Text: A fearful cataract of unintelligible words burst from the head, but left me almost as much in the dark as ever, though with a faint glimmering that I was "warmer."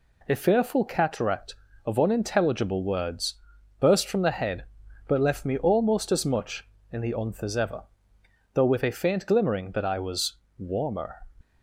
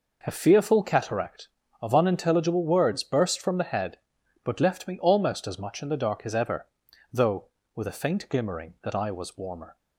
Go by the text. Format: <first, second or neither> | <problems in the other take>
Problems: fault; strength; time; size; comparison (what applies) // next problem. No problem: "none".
second | pauses between "words" and "burst"; noticeable; at 3.3 s; 0.46 s long // says "unth" for "dark"; at 7.1 s // pauses between "was" and "warmer"; slight; at 10.3 s; 0.22 s long